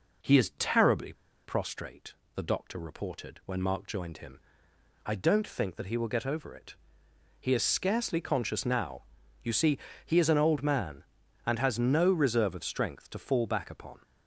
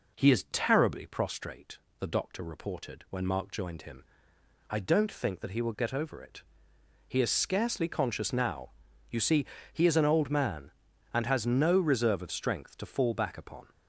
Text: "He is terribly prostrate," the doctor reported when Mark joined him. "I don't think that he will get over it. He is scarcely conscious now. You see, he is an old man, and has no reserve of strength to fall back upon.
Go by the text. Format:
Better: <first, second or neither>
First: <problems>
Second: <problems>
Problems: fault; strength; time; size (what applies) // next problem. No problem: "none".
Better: second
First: pauses between "terribly" and "prostrate"; slight; at 1.1 s; 0.32 s long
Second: none